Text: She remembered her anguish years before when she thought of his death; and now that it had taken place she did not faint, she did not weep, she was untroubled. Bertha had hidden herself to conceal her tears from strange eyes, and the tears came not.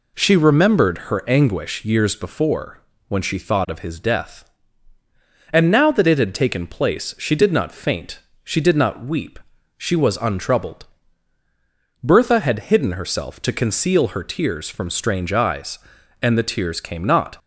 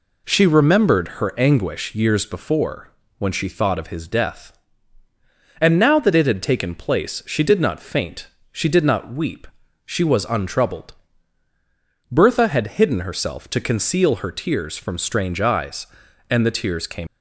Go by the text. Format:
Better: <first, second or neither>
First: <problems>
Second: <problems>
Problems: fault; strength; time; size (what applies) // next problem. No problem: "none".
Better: first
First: pauses between "before" and "when"; slight; at 2.7 s; 0.30 s long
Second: pauses between "before" and "when"; slight; at 2.8 s; 0.30 s long // stops before "not"; at 17.0 s